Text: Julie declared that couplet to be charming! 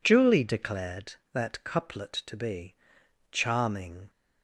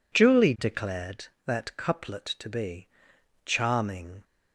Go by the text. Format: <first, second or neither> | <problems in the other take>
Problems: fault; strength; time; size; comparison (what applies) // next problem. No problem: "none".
neither | pauses between "be" and "charming"; noticeable; the same in both